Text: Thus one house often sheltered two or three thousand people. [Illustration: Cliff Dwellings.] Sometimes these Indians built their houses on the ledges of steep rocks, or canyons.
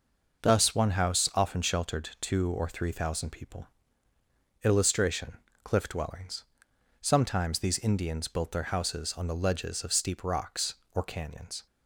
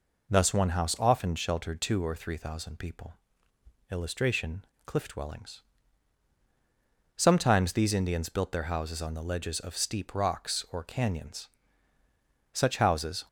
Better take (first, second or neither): first